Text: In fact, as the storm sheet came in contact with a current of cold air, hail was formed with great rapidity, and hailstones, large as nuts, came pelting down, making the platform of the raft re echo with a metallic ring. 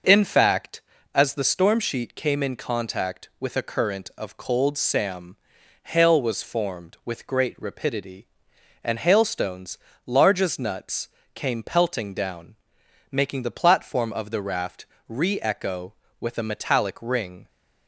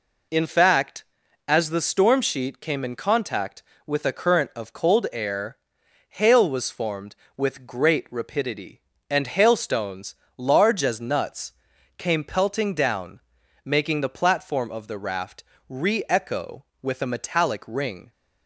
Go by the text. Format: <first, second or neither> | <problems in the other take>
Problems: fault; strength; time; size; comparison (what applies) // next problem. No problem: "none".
second | says "sam" for "air"; at 4.7 s // pauses between "raft" and "re"; slight; at 14.8 s; 0.24 s long; slight in the second